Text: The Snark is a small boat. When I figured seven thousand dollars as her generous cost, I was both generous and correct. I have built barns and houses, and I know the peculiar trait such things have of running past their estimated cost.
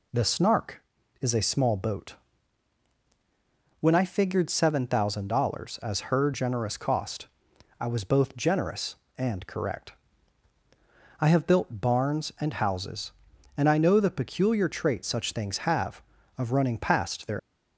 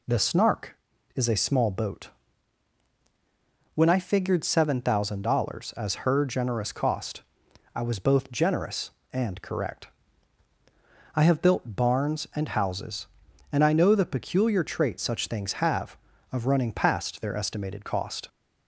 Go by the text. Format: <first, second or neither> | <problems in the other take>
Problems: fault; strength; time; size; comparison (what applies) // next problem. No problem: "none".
second | stops before "estimated cost"; at 17.3 s